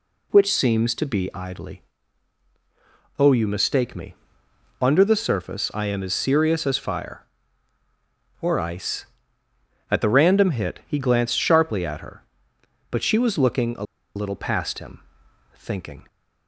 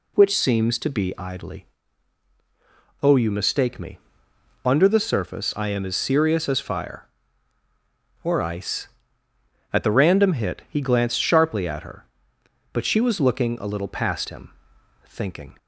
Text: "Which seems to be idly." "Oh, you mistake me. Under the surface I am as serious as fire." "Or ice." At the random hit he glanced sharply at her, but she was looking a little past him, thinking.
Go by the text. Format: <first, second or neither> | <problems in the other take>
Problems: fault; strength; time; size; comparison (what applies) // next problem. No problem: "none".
second | pauses between "a" and "little"; slight; at 13.8 s; 0.30 s long